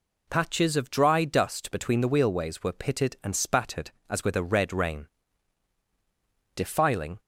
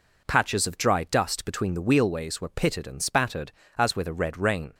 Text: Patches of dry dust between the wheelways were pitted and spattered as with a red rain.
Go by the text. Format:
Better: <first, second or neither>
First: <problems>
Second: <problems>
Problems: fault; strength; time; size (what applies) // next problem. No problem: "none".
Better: second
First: goes on to say "Defiling"; noticeable; from 6.5 s on; 0.64 s long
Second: none